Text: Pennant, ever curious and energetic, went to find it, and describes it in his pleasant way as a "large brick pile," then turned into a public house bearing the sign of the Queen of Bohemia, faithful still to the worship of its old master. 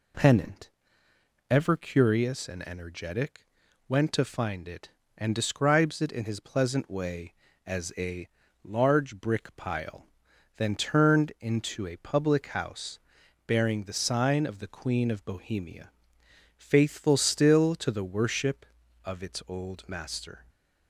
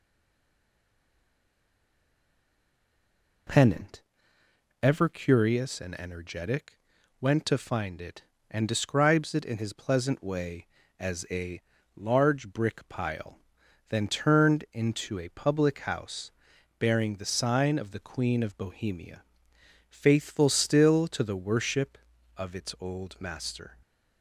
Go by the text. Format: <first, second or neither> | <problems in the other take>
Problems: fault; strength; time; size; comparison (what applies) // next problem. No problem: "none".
first | stays silent before the first word; strong; until 3.4 s; 3.4 s long // pauses between "a" and "large"; slight; at 11.6 s; 0.33 s long; slight in the first // pauses between "house" and "bearing"; noticeable; at 16.2 s; 0.50 s long; noticeable in the first